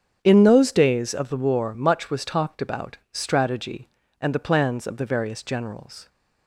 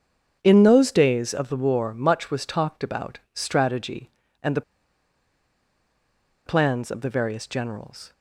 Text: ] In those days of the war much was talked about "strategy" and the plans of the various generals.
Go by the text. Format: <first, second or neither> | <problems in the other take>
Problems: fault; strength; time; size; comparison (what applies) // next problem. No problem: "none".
first | starts louder than the rest; strong; until 1.4 s; 7.5 dB; strong in the first // pauses between "the" and "plans"; strong; at 4.6 s; 1.8 s long